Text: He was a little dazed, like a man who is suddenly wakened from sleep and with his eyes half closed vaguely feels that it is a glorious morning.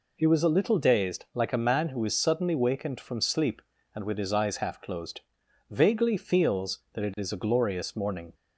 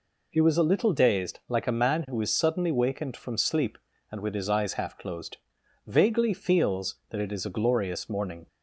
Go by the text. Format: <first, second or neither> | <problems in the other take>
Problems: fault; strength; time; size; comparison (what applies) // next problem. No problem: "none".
neither | pauses between "closed" and "vaguely"; noticeable; the same in both